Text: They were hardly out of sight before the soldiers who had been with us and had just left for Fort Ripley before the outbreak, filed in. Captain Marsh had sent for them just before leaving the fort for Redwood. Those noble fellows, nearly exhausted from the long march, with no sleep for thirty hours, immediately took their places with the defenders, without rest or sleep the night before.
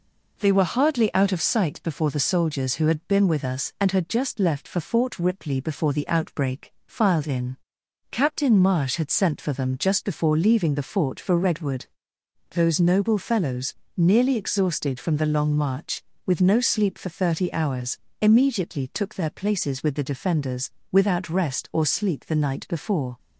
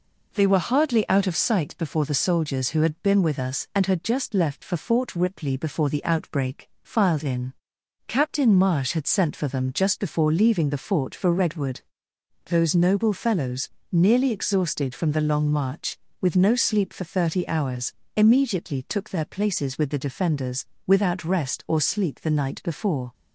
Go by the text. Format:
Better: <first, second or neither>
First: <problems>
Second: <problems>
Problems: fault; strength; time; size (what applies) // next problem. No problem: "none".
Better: neither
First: none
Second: none